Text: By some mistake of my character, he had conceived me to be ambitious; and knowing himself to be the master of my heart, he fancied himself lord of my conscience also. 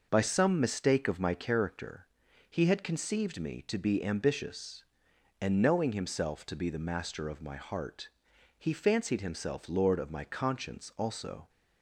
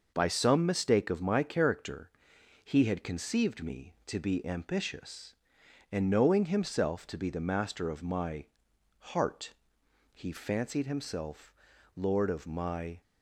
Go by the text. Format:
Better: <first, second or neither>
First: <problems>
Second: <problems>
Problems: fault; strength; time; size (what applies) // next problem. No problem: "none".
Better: first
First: none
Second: pauses between "my" and "heart"; noticeable; at 8.4 s; 0.52 s long // pauses between "himself" and "lord"; at 11.5 s; 0.42 s long // stops before "conscience also"; at 13.0 s